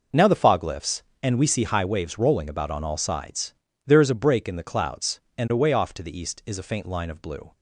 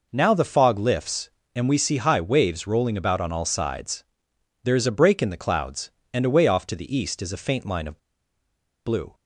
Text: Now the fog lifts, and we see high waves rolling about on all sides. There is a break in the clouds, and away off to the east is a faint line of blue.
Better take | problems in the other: first | pauses between "of" and "blue"; noticeable; at 7.9 s; 0.87 s long

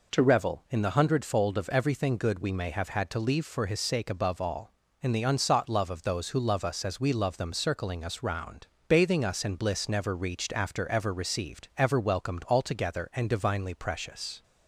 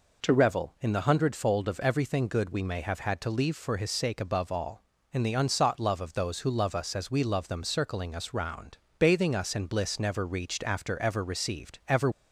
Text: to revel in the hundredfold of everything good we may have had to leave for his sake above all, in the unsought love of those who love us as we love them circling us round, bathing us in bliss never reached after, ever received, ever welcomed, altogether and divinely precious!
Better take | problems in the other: first | stops before "welcomed altogether and divinely precious"; at 12.1 s

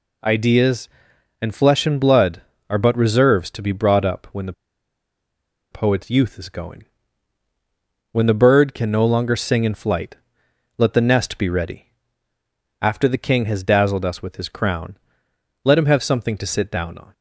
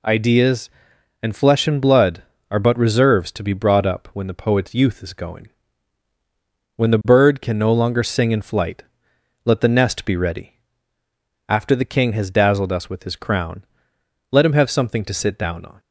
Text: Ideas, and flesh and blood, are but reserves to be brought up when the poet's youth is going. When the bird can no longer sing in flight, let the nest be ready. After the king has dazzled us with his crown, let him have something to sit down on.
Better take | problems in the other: second | pauses between "the" and "poet's"; at 4.5 s; 1.1 s long

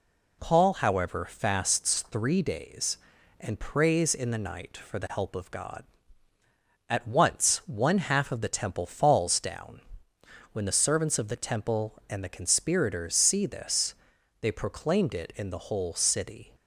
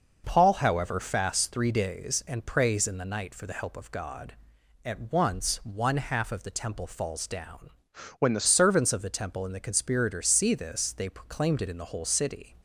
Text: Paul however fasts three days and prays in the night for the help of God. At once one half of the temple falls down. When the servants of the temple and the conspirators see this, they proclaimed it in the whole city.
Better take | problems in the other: first | changes voice from "When" to "the"; from 8.1 to 8.4 s; 0.3 s long

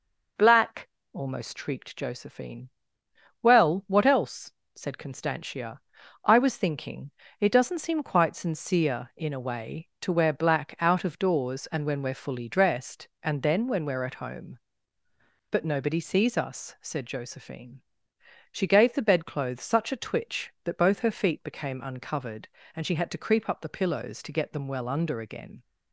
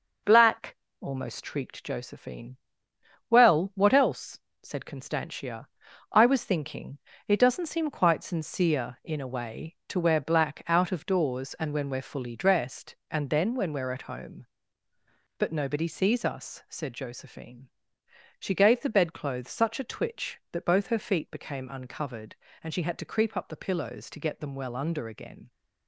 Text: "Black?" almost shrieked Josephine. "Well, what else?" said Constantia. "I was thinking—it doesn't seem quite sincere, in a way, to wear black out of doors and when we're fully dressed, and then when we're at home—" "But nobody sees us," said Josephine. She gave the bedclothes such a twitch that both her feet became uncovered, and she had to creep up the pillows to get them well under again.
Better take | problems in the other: first | gets quieter; noticeable; throughout; 4.5 dB

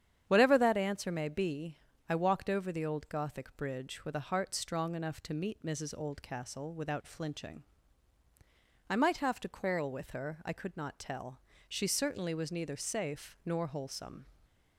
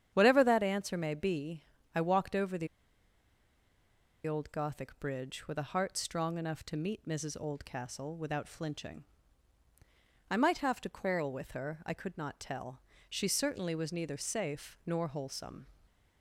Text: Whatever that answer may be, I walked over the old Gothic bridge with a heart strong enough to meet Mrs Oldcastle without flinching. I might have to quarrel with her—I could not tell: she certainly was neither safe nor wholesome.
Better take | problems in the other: first | starts louder than the rest; strong; until 1.1 s; 9 dB; strong in the first // pauses between "the" and "old"; strong; at 2.6 s; 1.5 s long

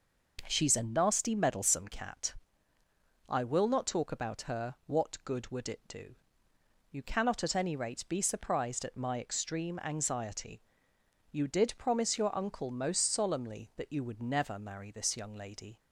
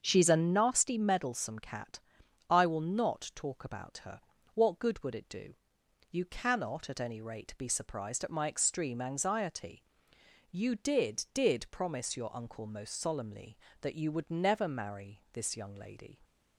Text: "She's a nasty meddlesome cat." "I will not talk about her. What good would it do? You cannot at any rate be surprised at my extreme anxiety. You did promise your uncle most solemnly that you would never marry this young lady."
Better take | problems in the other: first | starts louder than the rest; until 1.0 s; 7 dB // says "did" twice; at 11.3 s

